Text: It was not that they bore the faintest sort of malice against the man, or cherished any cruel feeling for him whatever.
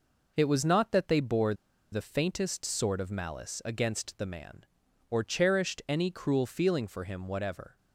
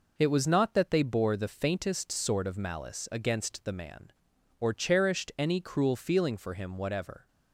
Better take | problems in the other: second | pauses between "bore" and "the"; at 1.5 s; 0.38 s long

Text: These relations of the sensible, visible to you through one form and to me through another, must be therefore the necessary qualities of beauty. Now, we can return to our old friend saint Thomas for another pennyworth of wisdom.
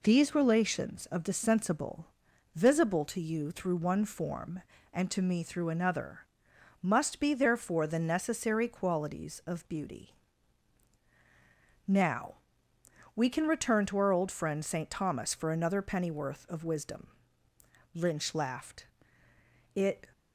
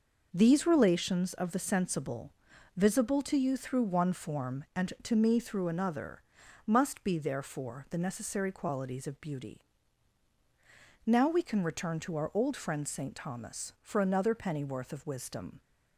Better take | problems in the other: second | goes on to say "Lynch laughed It"; strong; from 17.9 s on; 2.1 s long

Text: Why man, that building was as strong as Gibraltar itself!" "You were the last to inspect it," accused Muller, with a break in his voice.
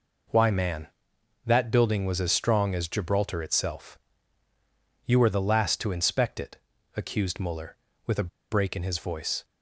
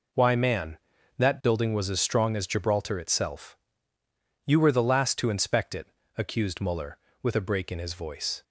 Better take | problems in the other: second | pauses between "a" and "break"; slight; at 8.2 s; 0.24 s long

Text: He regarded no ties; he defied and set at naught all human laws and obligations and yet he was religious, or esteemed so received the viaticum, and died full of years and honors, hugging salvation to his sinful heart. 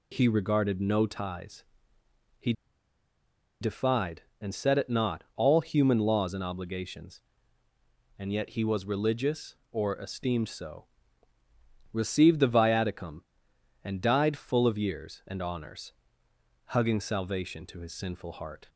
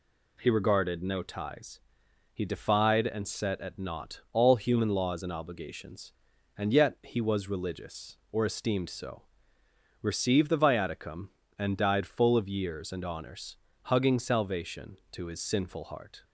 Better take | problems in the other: second | pauses between "he" and "defied"; at 2.5 s; 1.0 s long // pauses between "so" and "received"; at 10.8 s; 1.0 s long; noticeable in the second

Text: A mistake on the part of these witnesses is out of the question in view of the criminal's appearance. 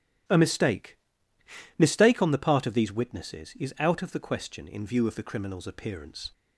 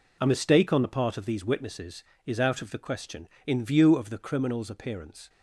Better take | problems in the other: second | starts louder than the rest; strong; until 2.0 s; 12.5 dB // says "mistake" twice; at 1.7 s

